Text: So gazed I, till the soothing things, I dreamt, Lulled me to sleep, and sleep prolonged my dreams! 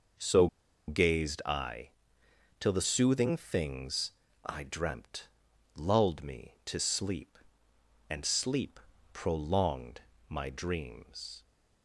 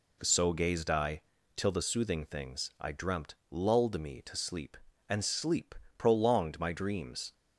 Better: second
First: pauses between "So" and "gazed"; at 0.4 s; 0.41 s long // pauses between "sleep" and "prolonged"; slight; at 8.7 s; 0.32 s long // pauses between "prolonged" and "my"; slight; at 9.9 s; 0.30 s long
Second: pauses between "sleep" and "prolonged"; slight; at 5.7 s; 0.22 s long

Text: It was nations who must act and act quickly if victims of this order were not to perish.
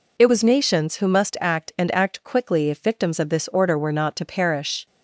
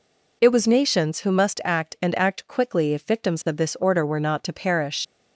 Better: first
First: none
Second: leaves "perish" unfinished; at 5.0 s; 80 ms

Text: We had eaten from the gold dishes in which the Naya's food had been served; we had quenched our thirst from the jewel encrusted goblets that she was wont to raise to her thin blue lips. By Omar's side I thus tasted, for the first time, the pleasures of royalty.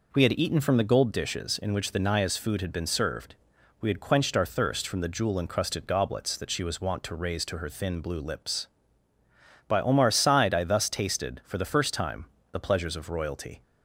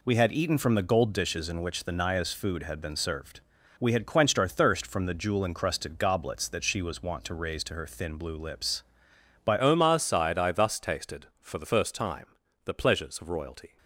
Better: first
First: none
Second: changes voice at "Omar's"; from 9.5 s on; 4.2 s long

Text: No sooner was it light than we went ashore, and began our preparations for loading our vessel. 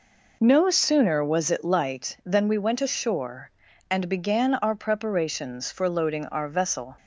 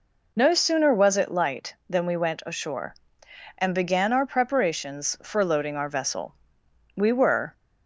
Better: first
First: none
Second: goes on to say "We were"; from 6.9 s on; 0.58 s long

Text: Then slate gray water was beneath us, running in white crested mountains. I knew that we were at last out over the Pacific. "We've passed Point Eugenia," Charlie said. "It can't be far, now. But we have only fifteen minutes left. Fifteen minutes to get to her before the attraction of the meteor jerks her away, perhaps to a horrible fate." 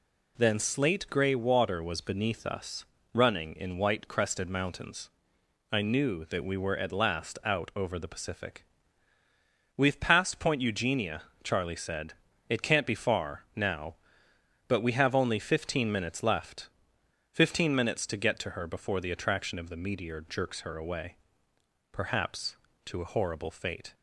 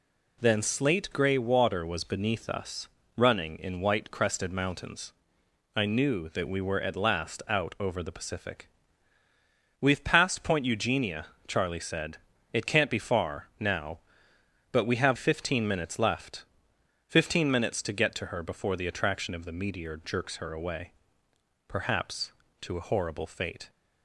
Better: first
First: none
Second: skips "only"; at 15.1 s

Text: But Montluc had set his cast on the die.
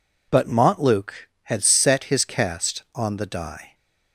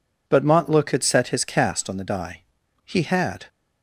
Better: first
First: none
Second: goes on to say "He had"; noticeable; from 2.8 s on; 0.62 s long

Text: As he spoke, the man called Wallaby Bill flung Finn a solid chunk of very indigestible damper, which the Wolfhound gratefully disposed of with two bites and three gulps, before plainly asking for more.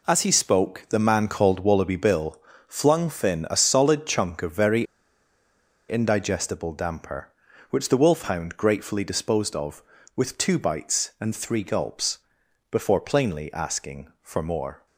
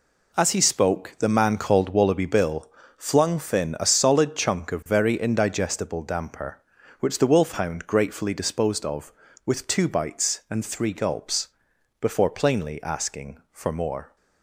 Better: second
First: pauses between "Bill" and "flung"; slight; at 2.3 s; 0.30 s long // pauses between "very" and "indigestible"; at 4.8 s; 1.0 s long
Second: pauses between "Bill" and "flung"; slight; at 2.6 s; 0.30 s long

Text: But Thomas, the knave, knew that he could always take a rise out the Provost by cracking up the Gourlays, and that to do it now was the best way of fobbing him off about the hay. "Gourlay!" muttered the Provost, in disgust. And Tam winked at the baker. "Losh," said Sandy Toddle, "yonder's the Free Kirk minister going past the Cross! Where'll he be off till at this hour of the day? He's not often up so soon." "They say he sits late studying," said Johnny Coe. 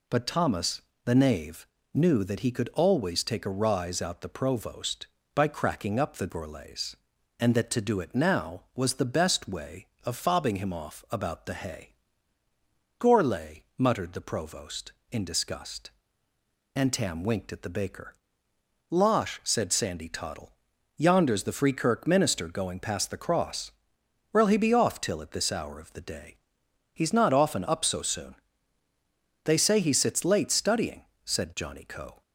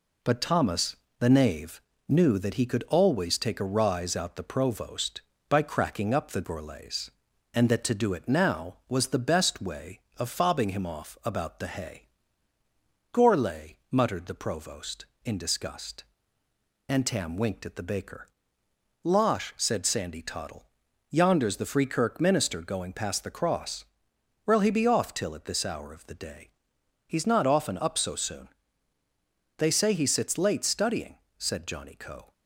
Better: first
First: none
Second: gets quieter; slight; throughout; 2.5 dB

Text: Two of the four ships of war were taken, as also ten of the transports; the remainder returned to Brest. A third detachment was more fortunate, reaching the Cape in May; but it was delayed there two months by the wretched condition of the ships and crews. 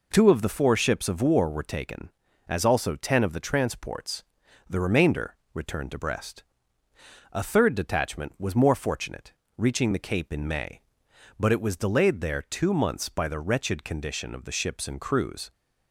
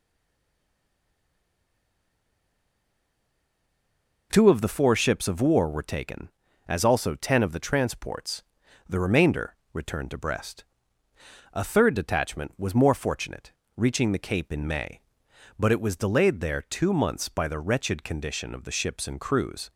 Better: first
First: pauses between "remainder" and "returned"; slight; at 5.3 s; 0.18 s long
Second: stays silent before the first word; strong; until 4.3 s; 4.3 s long // pauses between "remainder" and "returned"; slight; at 9.5 s; 0.18 s long

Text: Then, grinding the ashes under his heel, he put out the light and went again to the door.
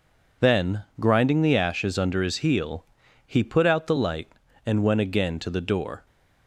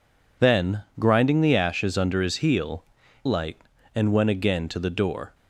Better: first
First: none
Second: skips "he put out the"; at 3.0 s

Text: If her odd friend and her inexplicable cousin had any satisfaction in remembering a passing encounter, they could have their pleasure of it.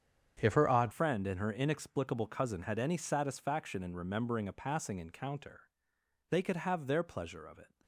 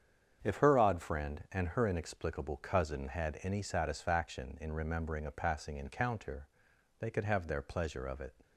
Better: second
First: starts louder than the rest; strong; until 1.4 s; 7.5 dB // changes voice at "friend"; from 0.9 s on; 6.8 s long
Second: starts louder than the rest; strong; until 1.4 s; 7.5 dB

